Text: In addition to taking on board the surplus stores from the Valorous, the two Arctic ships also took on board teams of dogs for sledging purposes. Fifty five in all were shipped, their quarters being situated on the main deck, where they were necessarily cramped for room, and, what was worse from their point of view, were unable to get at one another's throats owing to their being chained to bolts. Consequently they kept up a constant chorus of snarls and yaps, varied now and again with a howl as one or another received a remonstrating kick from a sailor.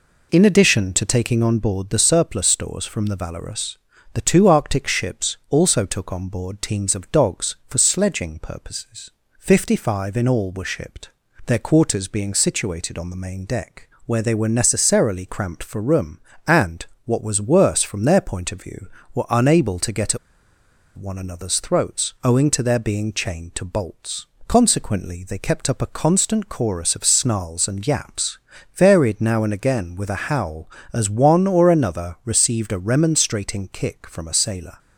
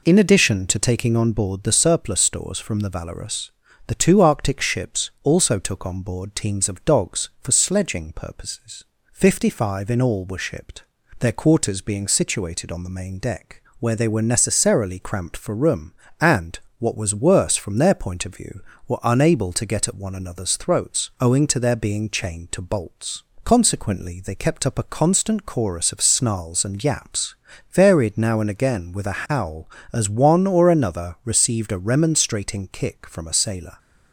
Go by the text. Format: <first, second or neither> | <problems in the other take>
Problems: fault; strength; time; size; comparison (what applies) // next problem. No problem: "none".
second | pauses between "at" and "one"; noticeable; at 20.1 s; 0.79 s long